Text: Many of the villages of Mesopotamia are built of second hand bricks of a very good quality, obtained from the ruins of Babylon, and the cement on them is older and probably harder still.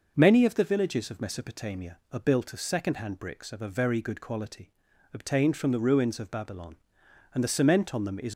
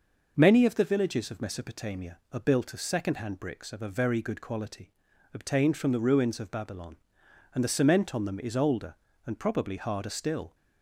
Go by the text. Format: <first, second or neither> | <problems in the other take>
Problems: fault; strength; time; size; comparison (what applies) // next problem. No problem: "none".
second | stops before "older and probably harder still"; at 8.3 s